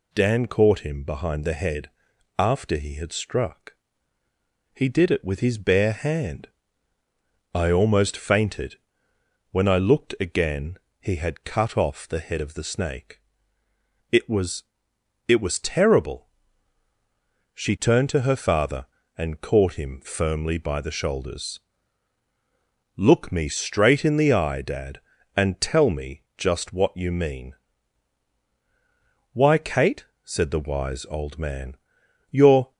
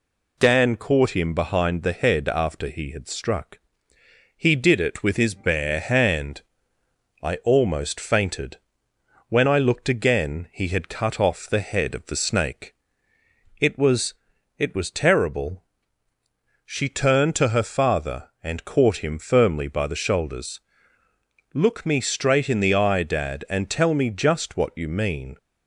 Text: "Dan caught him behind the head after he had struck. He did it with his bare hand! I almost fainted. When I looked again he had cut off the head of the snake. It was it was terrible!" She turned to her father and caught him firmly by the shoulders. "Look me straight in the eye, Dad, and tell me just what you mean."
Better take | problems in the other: second | pauses between "head" and "after"; noticeable; at 1.8 s; 0.48 s long // pauses between "again" and "he"; slight; at 10.7 s; 0.22 s long // pauses between "was" and "it"; noticeable; at 14.6 s; 0.64 s long; noticeable in the second // goes on to say "Why Kate said the wise old man you're"; strong; from 29.3 s on; 3.4 s long

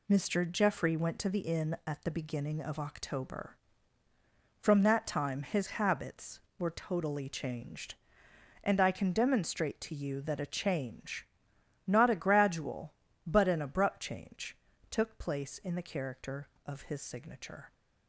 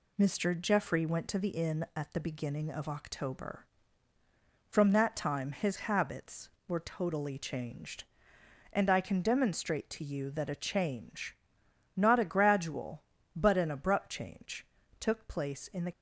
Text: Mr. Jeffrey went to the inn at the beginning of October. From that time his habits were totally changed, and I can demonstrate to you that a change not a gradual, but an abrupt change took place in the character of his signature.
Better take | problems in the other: first | pauses between "change" and "not"; noticeable; at 11.3 s; 0.60 s long; noticeable in the first // pauses between "change" and "took"; slight; at 14.6 s; 0.34 s long; slight in the first // stops before "character of his signature"; at 15.9 s

